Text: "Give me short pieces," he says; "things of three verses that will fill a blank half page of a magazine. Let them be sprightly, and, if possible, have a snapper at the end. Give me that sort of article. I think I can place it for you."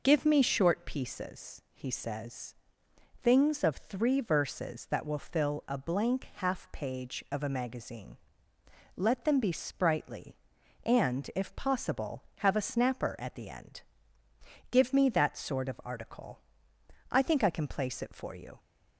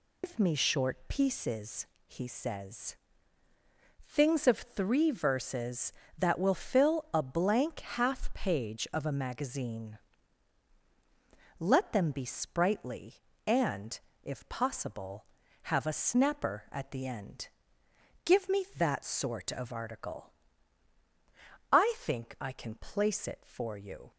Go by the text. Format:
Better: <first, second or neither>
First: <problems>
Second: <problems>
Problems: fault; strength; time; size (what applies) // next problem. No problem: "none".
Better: first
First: none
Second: loses the start of "Give"; at 0.2 s; 135 ms